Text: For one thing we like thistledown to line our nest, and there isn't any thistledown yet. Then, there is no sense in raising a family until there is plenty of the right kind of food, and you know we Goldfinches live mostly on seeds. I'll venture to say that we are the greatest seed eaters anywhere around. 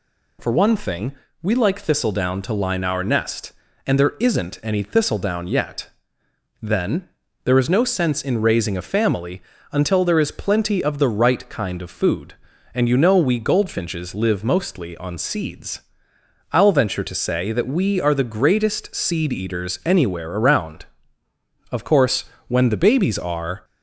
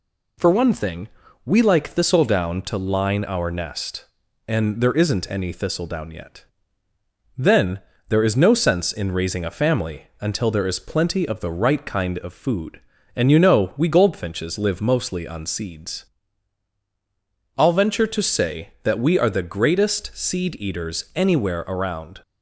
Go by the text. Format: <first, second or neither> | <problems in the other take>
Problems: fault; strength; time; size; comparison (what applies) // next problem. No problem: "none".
second | pauses between "thing" and "we"; slight; at 1.1 s; 0.28 s long; slight in the second // pauses between "family" and "until"; slight; at 9.4 s; 0.30 s long // goes on to say "Of course when the babies are"; strong; from 21.7 s on; 1.9 s long